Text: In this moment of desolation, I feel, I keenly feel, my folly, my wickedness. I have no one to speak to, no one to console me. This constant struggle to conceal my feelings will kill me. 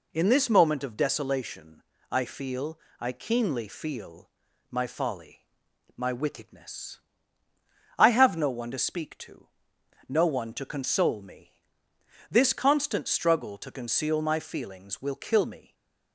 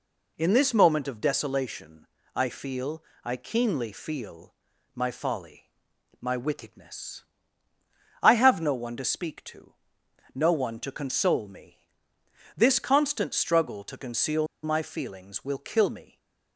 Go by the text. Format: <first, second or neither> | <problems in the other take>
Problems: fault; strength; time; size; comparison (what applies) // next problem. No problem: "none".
first | pauses between "conceal" and "my"; slight; at 14.4 s; 0.18 s long // stays silent after the last word; slight; from 16.0 s on; 0.5 s long; slight in the first